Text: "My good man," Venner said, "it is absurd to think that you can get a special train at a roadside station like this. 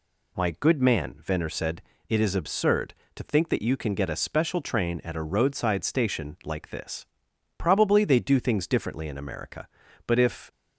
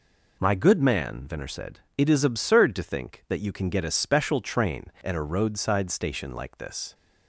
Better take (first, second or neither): second